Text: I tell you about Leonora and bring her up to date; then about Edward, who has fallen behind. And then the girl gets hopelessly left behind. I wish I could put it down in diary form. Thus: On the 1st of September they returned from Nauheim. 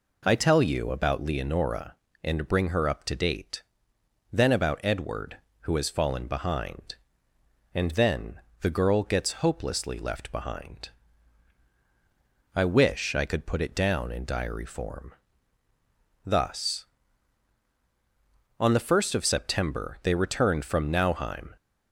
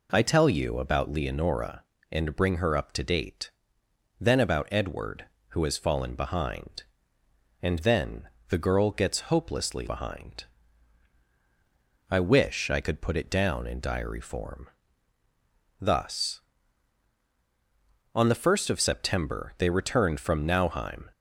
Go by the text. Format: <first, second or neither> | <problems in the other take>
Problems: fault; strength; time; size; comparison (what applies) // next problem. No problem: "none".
first | pauses between "then" and "the"; slight; at 8.2 s; 0.22 s long; slight in the first // skips "left"; at 9.8 s